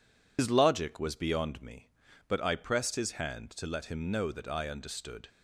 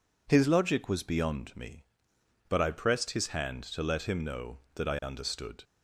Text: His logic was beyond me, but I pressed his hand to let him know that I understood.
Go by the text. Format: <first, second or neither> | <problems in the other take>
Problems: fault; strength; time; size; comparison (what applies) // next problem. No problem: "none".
second | loses the start of "His"; at 0.3 s; 95 ms